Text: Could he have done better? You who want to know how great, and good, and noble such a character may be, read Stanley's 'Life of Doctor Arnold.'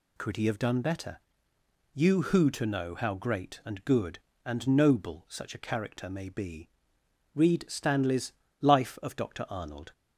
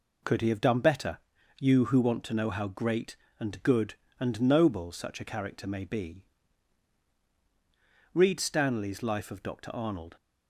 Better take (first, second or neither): second